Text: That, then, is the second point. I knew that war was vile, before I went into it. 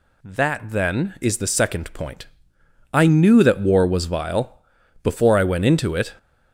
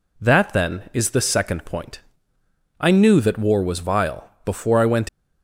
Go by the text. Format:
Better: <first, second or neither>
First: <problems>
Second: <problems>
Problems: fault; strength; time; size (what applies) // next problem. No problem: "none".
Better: first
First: none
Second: stops before "into it"; at 5.0 s